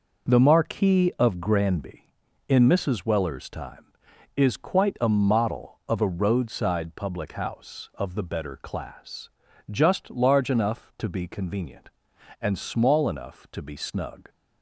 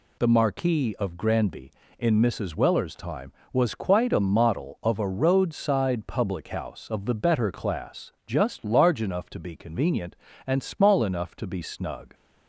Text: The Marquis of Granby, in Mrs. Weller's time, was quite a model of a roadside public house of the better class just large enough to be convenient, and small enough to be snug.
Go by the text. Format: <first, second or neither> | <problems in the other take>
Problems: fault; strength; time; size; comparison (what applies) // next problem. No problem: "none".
second | says "is" for "was"; at 4.3 s // pauses between "class" and "just"; at 9.2 s; 0.42 s long